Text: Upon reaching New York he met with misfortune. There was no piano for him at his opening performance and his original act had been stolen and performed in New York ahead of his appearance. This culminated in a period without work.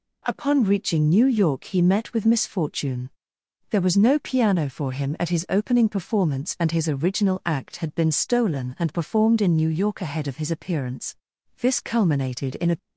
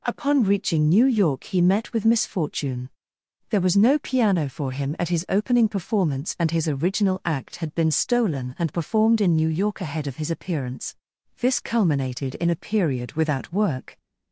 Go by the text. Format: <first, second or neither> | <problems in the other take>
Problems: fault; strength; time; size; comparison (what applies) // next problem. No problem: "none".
second | stops before "period without work"; at 12.7 s